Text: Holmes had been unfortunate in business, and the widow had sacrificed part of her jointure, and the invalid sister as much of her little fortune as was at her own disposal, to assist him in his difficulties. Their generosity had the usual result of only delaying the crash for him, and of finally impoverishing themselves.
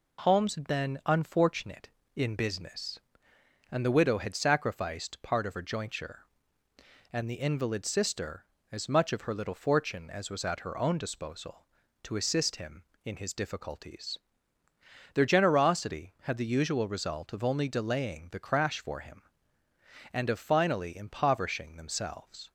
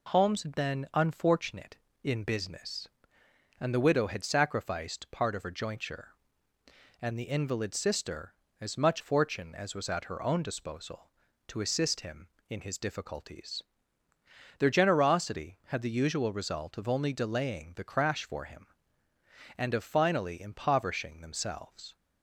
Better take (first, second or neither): first